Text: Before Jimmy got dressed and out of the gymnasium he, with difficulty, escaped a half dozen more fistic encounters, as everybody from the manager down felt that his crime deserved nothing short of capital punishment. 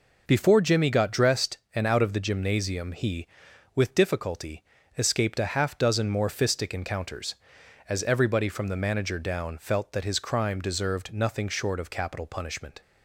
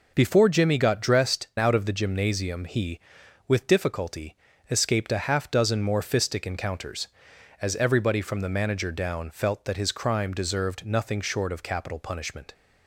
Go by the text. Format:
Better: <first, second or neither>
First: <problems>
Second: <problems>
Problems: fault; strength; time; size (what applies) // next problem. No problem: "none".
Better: first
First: none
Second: skips "and"; at 1.5 s